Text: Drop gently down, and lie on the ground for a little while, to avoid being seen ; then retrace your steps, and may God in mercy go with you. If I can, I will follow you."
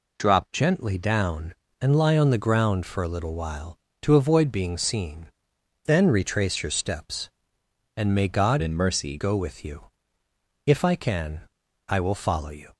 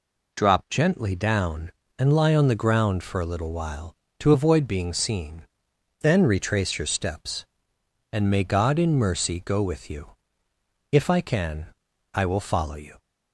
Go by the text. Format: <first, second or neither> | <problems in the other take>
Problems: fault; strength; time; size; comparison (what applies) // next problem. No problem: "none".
second | changes voice from "in" to "mercy"; from 8.6 to 9.1 s; 0.5 s long